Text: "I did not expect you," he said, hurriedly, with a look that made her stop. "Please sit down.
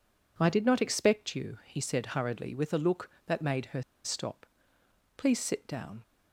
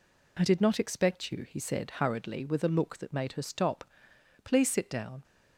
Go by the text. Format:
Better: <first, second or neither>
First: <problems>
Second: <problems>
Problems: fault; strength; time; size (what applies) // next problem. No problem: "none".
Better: second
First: pauses between "her" and "stop"; slight; at 3.8 s; 0.23 s long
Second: none